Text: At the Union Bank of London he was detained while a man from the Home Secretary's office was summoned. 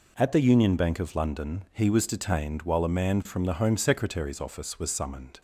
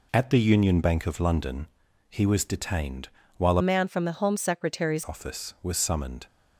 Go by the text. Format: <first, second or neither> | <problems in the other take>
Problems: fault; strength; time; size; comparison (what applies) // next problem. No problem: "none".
first | pauses between "London" and "he"; at 1.6 s; 0.42 s long // pauses between "detained" and "while"; slight; at 3.0 s; 0.28 s long // changes voice from "man" to "Secretary's"; from 3.6 to 5.0 s; 1.4 s long